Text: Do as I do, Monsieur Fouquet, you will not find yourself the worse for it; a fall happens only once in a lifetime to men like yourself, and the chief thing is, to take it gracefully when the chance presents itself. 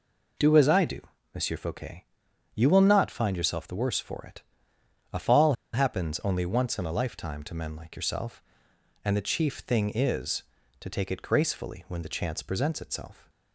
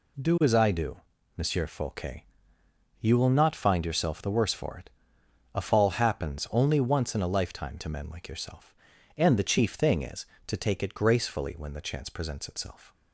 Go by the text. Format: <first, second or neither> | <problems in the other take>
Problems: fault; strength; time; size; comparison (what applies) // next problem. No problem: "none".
second | pauses between "fall" and "happens"; slight; at 5.5 s; 0.20 s long